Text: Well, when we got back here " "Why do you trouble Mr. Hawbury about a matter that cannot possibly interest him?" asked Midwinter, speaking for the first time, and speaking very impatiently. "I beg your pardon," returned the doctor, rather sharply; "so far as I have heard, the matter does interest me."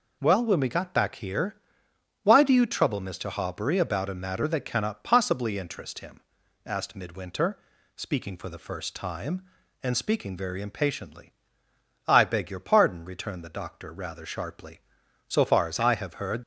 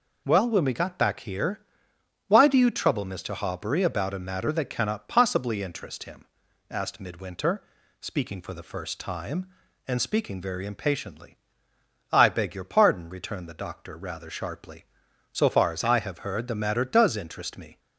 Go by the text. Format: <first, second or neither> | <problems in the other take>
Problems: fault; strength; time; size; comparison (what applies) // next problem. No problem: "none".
second | stops before "the matter does interest me"; at 16.4 s